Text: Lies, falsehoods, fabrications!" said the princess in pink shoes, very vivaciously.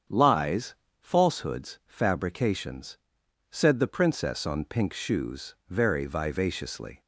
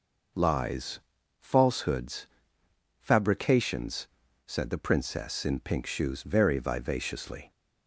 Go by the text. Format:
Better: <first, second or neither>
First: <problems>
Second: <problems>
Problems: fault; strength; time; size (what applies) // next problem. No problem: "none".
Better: second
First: starts louder than the rest; strong; until 1.3 s; 7.5 dB // says "on" for "in"; at 4.4 s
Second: none